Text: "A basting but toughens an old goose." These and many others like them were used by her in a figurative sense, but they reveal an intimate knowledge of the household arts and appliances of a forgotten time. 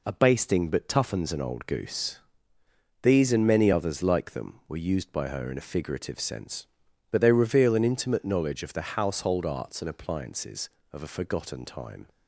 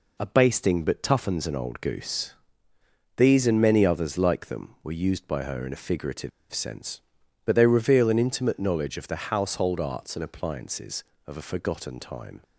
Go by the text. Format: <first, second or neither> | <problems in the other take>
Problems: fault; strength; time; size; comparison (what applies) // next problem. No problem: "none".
first | pauses between "figurative" and "sense"; slight; at 6.3 s; 0.22 s long